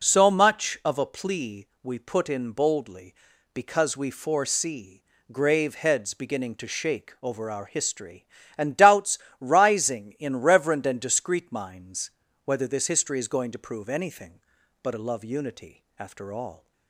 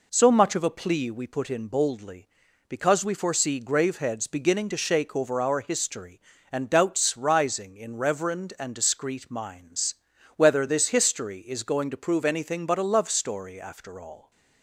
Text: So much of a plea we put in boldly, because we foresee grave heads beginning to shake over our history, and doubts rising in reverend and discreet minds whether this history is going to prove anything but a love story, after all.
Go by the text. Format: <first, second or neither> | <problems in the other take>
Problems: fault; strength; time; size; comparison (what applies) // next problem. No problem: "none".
second | pauses between "foresee" and "grave"; slight; at 5.0 s; 0.26 s long // pauses between "doubts" and "rising"; slight; at 9.1 s; 0.22 s long // pauses between "minds" and "whether"; slight; at 12.1 s; 0.34 s long; also in the second // says "unity" for "story"; at 15.2 s